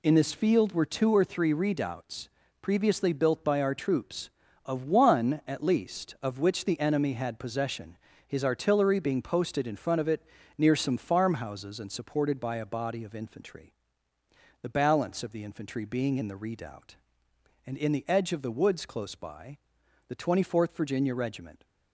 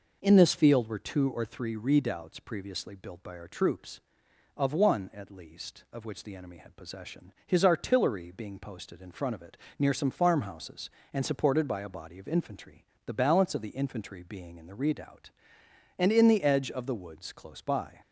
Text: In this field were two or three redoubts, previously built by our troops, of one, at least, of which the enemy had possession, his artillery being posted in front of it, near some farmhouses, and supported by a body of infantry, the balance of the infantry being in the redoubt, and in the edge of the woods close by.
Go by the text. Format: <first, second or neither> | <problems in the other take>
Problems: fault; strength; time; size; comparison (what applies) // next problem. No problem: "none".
second | goes on to say "The Twenty fourth Virginia Regiment"; from 20.0 s on; 1.5 s long